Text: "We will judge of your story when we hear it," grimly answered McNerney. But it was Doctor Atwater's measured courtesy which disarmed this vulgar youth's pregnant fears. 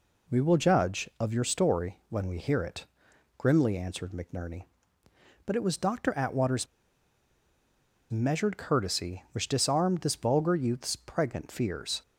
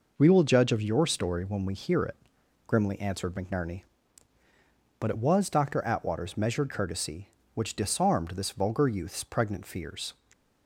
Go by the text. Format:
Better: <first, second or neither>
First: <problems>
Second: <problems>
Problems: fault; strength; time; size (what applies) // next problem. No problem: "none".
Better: second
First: pauses between "Atwater's" and "measured"; strong; at 6.6 s; 1.4 s long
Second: none